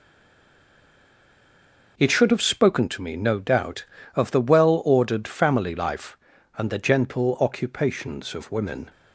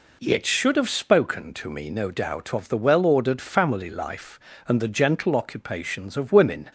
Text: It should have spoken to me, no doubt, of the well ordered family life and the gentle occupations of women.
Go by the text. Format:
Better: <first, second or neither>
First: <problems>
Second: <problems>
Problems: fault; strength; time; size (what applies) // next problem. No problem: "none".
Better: second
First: stays silent before the first word; noticeable; until 1.9 s; 1.9 s long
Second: none